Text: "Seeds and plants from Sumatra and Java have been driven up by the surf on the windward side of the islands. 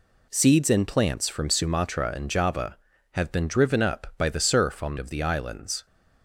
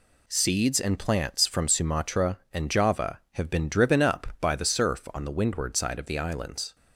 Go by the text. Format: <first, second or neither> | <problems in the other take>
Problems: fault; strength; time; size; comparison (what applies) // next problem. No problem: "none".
second | skips "the windward side"; at 4.9 s